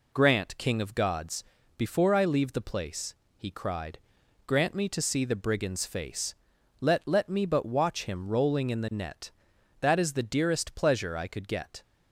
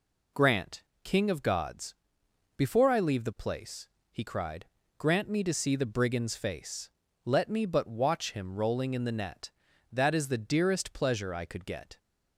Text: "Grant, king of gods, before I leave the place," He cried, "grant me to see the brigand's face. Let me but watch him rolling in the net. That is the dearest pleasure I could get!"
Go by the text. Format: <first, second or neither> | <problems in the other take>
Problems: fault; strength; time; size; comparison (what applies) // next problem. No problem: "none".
second | says "Let" twice; at 7.0 s